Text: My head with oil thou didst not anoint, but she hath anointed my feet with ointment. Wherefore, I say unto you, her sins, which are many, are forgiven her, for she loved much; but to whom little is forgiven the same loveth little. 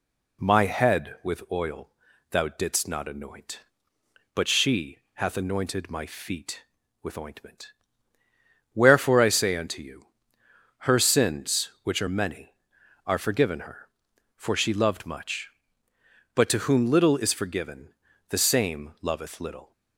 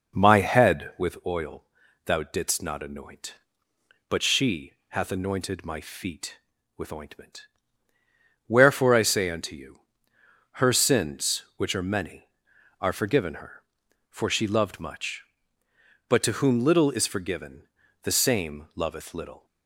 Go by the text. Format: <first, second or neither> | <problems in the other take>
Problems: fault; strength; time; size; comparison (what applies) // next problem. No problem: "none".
first | starts louder than the rest; noticeable; until 1.2 s; 5.5 dB // pauses between "oil" and "thou"; at 1.6 s; 0.42 s long; also in the first // pauses between "she" and "hath"; slight; at 4.7 s; 0.16 s long; slight in the first // pauses between "forgiven" and "the"; slight; at 17.6 s; 0.34 s long; slight in the first